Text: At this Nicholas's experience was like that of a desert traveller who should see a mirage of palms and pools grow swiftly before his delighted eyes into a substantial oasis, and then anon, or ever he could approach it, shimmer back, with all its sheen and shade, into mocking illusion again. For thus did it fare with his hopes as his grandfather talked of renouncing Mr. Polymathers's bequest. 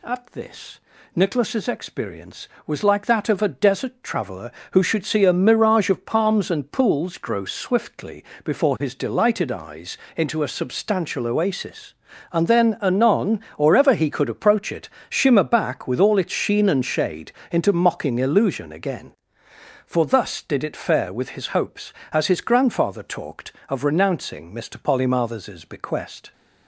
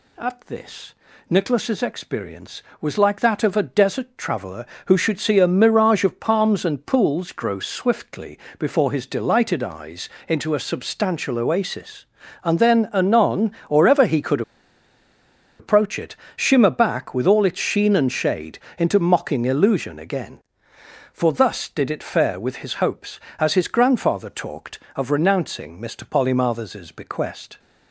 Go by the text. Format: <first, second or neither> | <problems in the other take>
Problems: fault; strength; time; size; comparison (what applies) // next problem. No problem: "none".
first | pauses between "this" and "Nicholas's"; slight; at 0.9 s; 0.36 s long; slight in the first // pauses between "swiftly" and "before"; slight; at 8.3 s; 0.22 s long; slight in the first // pauses between "eyes" and "into"; slight; at 10.0 s; 0.18 s long; slight in the first // pauses between "could" and "approach"; at 14.4 s; 1.1 s long